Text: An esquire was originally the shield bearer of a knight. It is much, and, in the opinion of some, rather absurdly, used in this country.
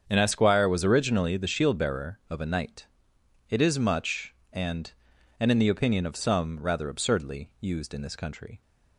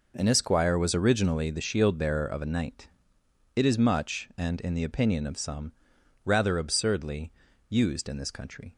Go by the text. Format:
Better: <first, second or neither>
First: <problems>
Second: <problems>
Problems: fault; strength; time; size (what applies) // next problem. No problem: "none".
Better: second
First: starts louder than the rest; strong; until 1.0 s; 7.5 dB // says "and" twice; at 5.3 s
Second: none